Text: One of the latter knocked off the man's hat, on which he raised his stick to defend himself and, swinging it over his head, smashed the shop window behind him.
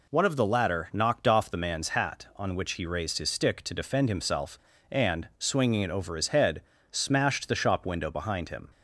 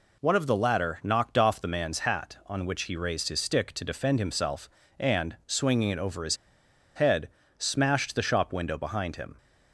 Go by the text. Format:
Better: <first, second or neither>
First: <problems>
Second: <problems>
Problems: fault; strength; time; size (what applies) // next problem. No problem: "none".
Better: first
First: none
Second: pauses between "his" and "head"; noticeable; at 6.3 s; 0.59 s long